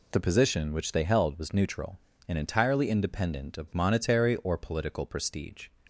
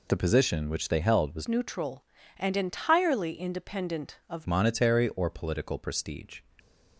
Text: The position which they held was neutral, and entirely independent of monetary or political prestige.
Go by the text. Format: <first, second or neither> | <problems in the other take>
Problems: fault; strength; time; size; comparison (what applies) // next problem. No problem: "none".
first | changes voice from "neutral" to "of"; from 1.4 to 4.4 s; 3.0 s long